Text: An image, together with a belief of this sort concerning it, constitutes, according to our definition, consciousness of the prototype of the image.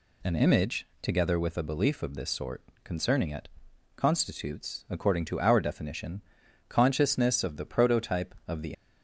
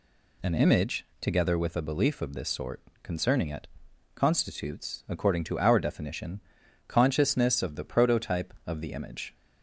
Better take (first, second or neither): second